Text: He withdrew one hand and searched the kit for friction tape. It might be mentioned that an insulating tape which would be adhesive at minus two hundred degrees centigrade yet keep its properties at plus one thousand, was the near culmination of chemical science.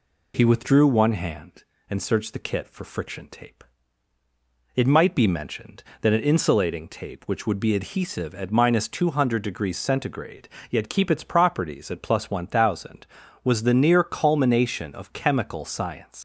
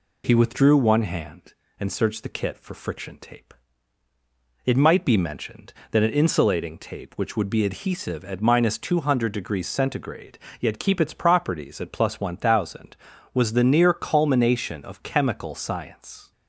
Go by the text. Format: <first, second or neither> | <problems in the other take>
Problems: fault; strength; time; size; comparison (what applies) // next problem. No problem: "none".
second | pauses between "centigrade" and "yet"; slight; at 10.4 s; 0.20 s long; slight in the second // leaves "science" unfinished; at 16.1 s; 185 ms